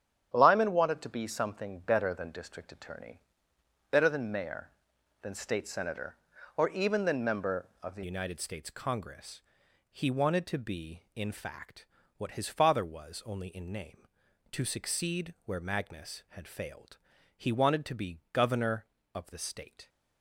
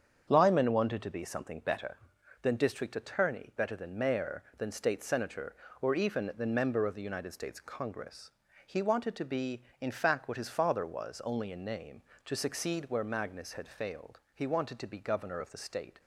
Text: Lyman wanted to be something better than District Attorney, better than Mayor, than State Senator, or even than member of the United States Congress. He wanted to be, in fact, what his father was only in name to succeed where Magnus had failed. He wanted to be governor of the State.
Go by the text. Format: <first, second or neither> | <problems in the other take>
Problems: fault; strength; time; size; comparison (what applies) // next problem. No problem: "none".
second | starts louder than the rest; strong; until 1.3 s; 9.5 dB; strong in the second // changes voice at "United"; from 8.0 s on; 11.8 s long